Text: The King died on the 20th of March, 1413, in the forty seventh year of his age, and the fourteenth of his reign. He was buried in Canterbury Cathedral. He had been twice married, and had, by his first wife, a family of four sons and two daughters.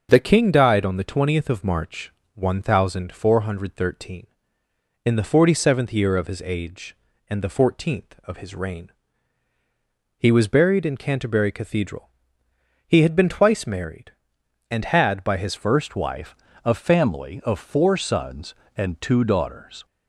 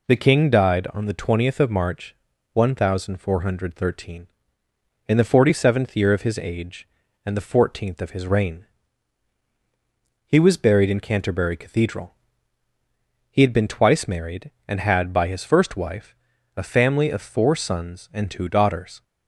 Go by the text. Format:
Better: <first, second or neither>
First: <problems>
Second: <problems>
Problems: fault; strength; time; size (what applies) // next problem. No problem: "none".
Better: second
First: starts louder than the rest; until 1.1 s; 6.5 dB // changes voice at "first"; from 15.5 s on; 4.3 s long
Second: none